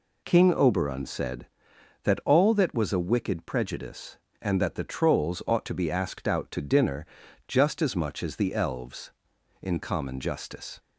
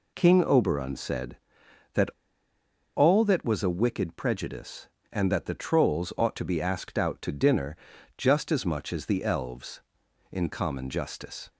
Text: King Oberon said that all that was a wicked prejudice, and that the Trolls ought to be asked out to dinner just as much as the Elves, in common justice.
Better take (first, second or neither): first